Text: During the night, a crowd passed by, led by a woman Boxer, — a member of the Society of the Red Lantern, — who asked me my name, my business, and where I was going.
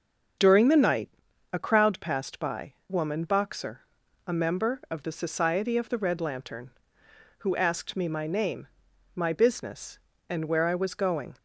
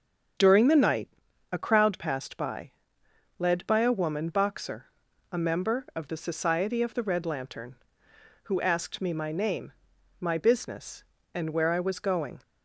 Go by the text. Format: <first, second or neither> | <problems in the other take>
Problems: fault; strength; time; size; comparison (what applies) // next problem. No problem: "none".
second | starts louder than the rest; until 1.8 s; 7 dB; strong in the second // skips "led by a"; at 2.8 s